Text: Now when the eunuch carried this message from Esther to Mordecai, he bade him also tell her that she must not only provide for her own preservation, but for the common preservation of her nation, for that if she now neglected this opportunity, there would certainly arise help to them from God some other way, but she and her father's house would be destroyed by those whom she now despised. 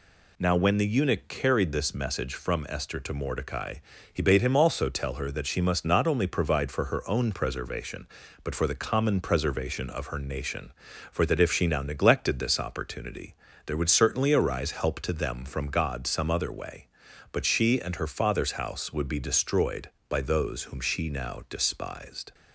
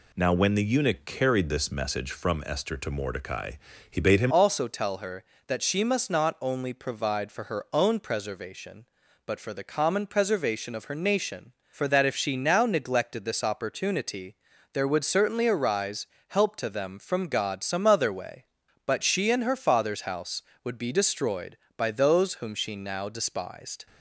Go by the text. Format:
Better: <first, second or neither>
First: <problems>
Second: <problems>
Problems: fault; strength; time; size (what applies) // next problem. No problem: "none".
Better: first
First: none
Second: changes voice at "also"; from 4.2 s on; 19.6 s long // pauses between "arise" and "help"; slight; at 16.0 s; 0.22 s long